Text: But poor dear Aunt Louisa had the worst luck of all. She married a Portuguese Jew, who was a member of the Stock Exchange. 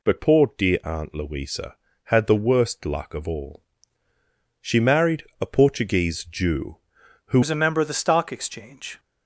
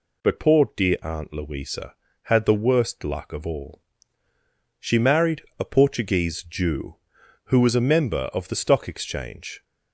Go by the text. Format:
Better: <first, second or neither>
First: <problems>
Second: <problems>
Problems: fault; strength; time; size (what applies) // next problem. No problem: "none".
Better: second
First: pauses between "married" and "a"; slight; at 5.2 s; 0.16 s long // changes voice at "was"; from 7.4 s on; 1.5 s long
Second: pauses between "married" and "a"; slight; at 5.4 s; 0.16 s long